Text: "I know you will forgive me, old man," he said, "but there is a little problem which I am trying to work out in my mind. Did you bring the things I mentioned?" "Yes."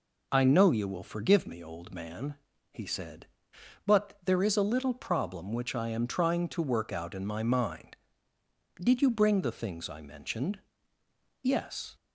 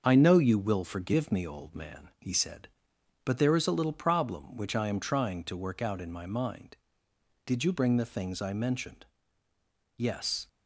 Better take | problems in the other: first | gets quieter; noticeable; throughout; 5 dB

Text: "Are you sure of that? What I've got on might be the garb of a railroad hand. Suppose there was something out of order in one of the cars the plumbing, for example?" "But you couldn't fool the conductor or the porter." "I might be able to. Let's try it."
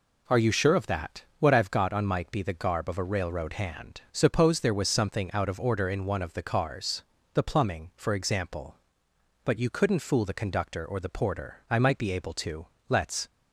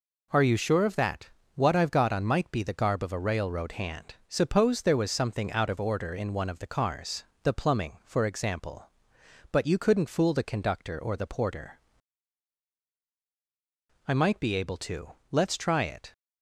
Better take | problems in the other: second | pauses between "cars" and "the"; slight; at 7.0 s; 0.32 s long; slight in the second // stops before "try it"; at 13.2 s

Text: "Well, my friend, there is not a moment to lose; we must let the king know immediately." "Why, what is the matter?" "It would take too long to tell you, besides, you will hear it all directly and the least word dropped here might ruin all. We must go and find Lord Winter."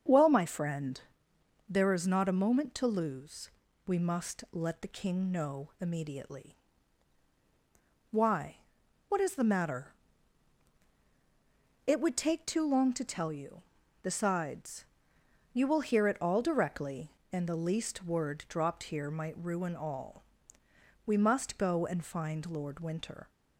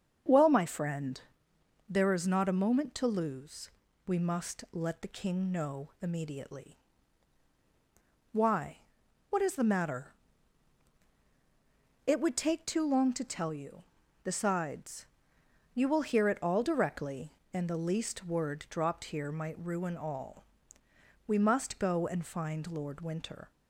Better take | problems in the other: neither | starts louder than the rest; the same in both

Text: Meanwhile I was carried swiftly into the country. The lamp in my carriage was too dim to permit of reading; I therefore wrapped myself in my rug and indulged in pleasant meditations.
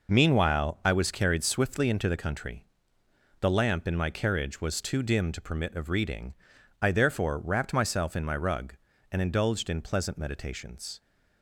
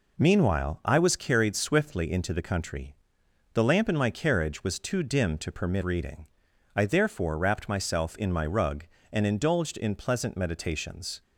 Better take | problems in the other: first | skips "of"; at 5.8 s

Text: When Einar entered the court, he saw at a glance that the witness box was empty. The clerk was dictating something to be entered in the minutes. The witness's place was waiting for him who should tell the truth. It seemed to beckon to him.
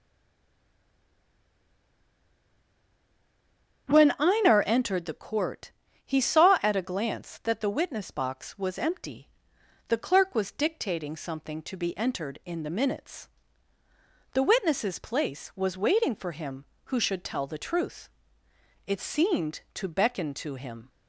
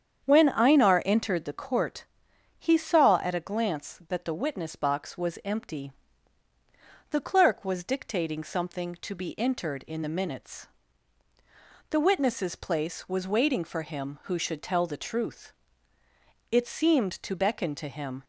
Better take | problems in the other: second | stays silent before the first word; strong; until 3.8 s; 3.8 s long // starts louder than the rest; strong; until 4.9 s; 8 dB; strong in the second

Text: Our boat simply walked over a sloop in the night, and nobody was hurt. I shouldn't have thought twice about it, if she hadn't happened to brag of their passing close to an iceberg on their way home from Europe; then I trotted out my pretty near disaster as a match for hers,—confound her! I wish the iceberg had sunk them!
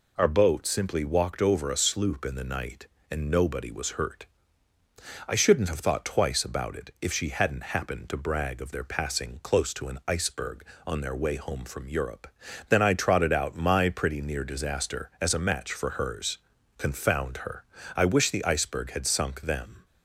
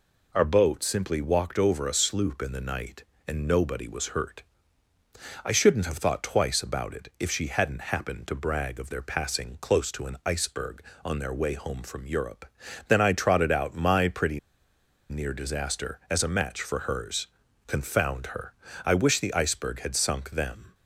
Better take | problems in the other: first | pauses between "pretty" and "near"; noticeable; at 14.3 s; 0.70 s long

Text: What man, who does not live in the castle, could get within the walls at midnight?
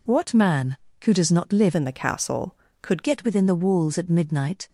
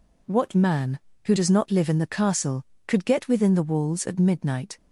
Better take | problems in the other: second | changes voice from "in" to "could"; from 1.7 to 3.0 s; 1.3 s long

